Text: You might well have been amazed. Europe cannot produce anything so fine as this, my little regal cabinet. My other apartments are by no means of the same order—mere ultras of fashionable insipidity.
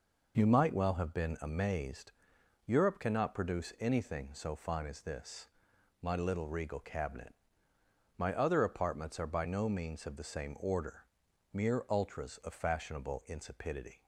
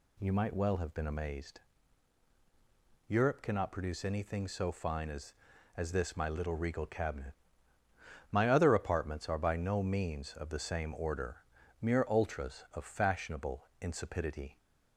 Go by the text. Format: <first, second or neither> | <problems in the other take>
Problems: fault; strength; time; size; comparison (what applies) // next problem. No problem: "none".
first | says "as" twice; at 5.7 s